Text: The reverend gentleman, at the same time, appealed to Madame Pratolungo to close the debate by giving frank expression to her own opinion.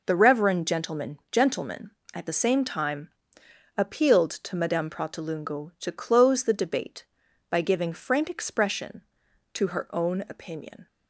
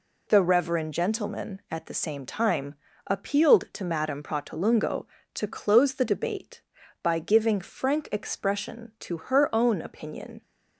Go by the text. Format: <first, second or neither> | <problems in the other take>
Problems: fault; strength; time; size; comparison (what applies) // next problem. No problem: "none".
second | says "gentleman" twice; at 1.3 s